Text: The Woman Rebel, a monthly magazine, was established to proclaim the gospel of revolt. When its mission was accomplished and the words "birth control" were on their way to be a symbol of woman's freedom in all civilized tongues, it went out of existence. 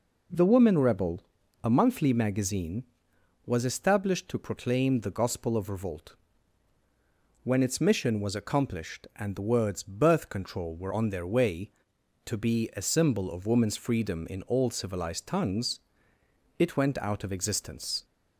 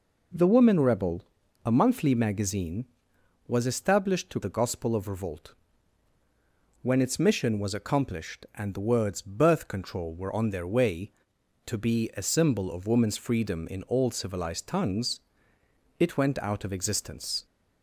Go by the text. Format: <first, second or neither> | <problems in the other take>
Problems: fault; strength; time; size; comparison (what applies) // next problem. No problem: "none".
first | skips "proclaim"; at 4.4 s